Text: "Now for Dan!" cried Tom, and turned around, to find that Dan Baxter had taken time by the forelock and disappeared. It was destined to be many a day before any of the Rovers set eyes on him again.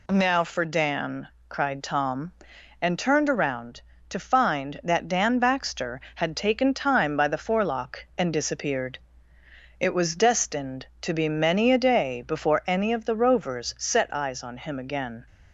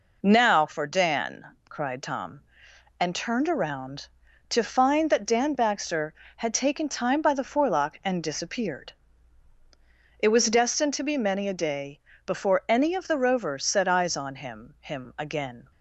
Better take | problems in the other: first | pauses between "day" and "before"; slight; at 12.0 s; 0.26 s long // says "him" twice; at 14.7 s

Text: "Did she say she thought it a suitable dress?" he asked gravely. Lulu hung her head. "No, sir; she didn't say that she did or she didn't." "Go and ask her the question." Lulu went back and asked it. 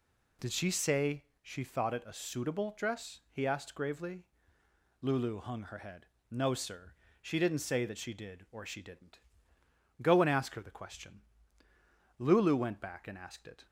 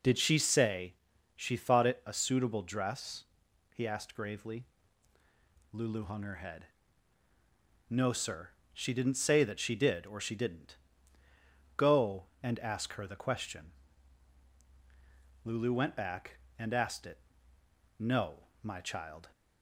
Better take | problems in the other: first | pauses between "say" and "she"; at 0.9 s; 0.40 s long; slight in the first // goes on to say "No my child"; noticeable; from 17.9 s on; 1.3 s long

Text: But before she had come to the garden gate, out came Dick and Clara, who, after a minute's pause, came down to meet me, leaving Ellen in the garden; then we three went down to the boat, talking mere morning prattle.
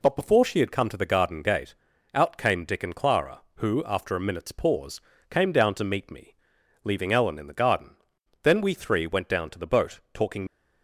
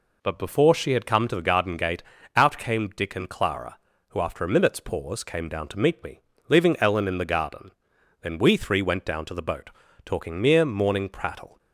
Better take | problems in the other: second | stops before "mere morning prattle"; at 10.4 s

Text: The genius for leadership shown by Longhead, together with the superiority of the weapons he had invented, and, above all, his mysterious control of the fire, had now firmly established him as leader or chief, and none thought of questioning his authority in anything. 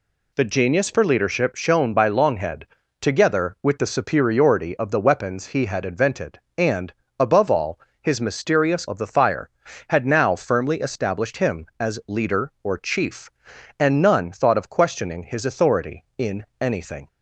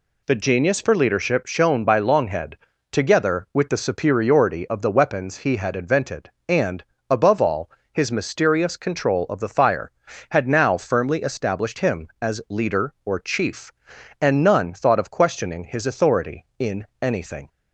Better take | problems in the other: second | skips "control"; at 8.8 s

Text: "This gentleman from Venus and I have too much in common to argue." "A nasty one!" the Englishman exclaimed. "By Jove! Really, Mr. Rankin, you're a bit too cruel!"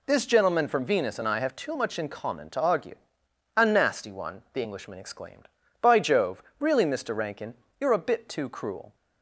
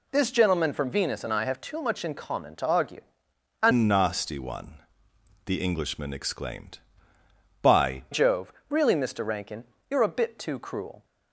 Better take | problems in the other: first | changes voice from "nasty" to "By"; from 3.7 to 8.0 s; 4.3 s long

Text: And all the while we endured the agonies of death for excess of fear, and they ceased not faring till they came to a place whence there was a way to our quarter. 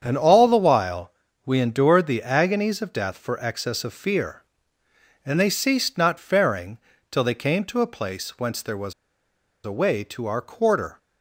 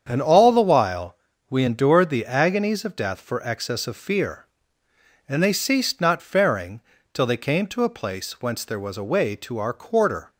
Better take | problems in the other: second | starts louder than the rest; strong; until 1.0 s; 7.5 dB; strong in the second // pauses between "while" and "we"; slight; at 1.1 s; 0.34 s long; slight in the second // pauses between "faring" and "till"; slight; at 6.7 s; 0.32 s long; slight in the second // pauses between "was" and "a"; noticeable; at 8.9 s; 0.72 s long

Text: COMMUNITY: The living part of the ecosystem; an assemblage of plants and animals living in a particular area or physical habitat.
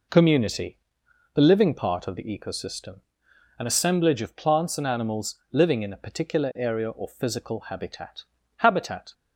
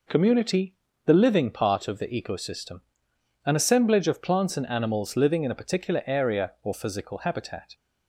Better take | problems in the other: second | says "habitat" twice; at 8.5 s

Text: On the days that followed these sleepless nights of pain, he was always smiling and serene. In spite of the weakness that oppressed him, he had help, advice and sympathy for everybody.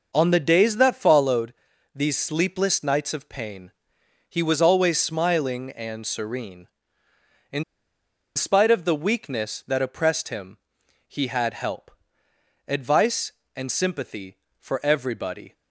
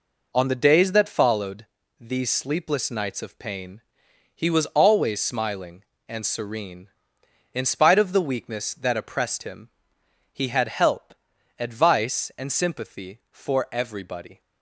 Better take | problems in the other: second | pauses between "followed" and "these"; at 1.5 s; 0.42 s long; slight in the second // pauses between "In" and "spite"; noticeable; at 7.6 s; 0.72 s long

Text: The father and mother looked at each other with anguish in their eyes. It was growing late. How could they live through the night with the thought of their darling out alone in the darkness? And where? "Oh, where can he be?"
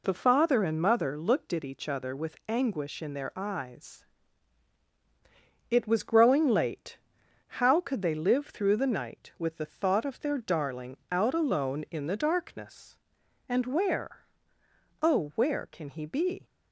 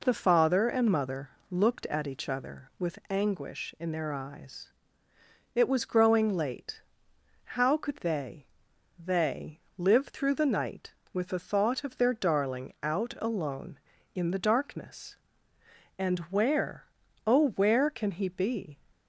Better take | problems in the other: first | pauses between "mother" and "looked"; slight; at 1.3 s; 0.18 s long // says "they" twice; at 8.9 s

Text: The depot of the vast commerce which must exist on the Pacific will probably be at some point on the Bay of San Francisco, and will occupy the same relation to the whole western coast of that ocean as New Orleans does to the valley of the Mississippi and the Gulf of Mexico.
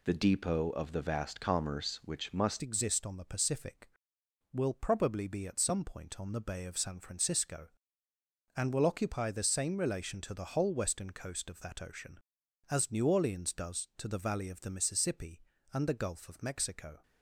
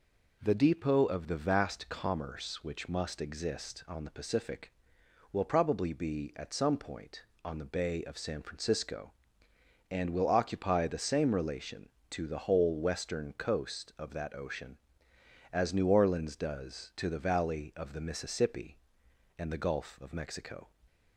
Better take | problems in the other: second | changes voice at "exist"; from 2.6 s on; 14.4 s long

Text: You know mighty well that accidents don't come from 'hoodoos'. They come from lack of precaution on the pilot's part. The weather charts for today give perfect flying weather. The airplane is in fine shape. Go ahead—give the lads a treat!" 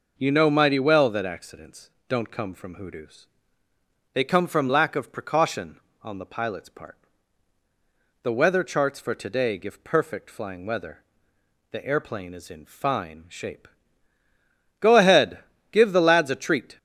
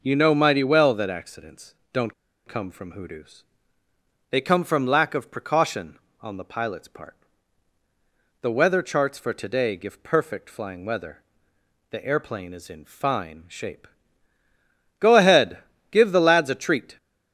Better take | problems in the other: first | pauses between "accidents" and "don't"; slight; at 1.7 s; 0.18 s long; slight in the first // pauses between "don't" and "come"; slight; at 2.1 s; 0.35 s long

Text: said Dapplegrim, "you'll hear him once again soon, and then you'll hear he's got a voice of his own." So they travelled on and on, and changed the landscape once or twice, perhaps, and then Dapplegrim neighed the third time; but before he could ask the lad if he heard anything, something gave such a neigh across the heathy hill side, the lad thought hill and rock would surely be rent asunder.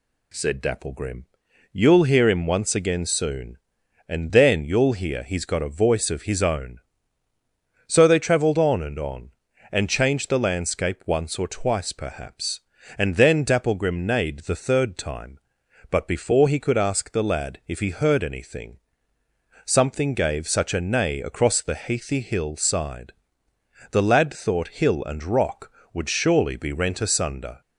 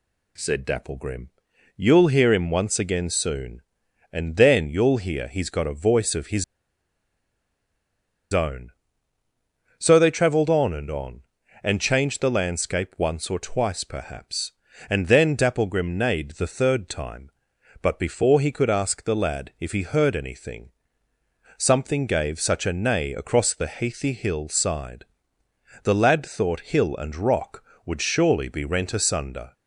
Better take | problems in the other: first | pauses between "his" and "own"; strong; at 6.4 s; 1.8 s long

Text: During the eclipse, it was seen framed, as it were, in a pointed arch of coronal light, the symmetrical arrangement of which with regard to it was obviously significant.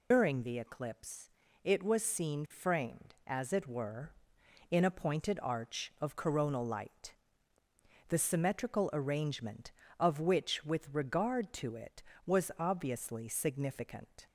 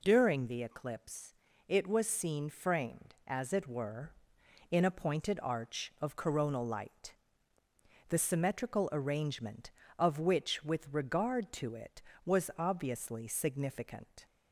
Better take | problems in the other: second | loses the start of "During"; at 0.1 s; 115 ms

